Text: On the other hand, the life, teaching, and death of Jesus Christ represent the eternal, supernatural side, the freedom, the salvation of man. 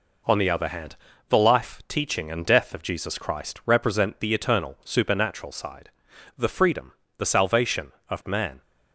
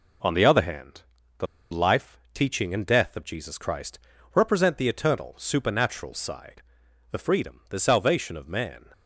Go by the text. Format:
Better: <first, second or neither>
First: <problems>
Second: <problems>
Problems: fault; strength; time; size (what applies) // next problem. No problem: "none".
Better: first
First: none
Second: pauses between "the" and "life"; slight; at 1.4 s; 0.25 s long // pauses between "Christ" and "represent"; slight; at 3.9 s; 0.36 s long